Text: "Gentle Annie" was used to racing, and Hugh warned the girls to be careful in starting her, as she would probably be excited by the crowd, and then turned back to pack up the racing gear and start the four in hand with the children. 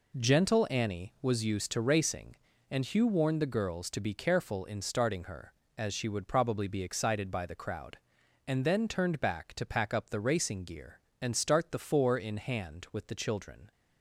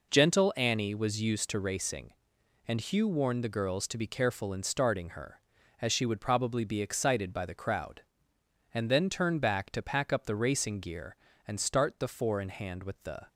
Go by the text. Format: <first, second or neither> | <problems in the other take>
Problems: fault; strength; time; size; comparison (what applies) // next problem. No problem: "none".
first | stops before "children"; at 13.2 s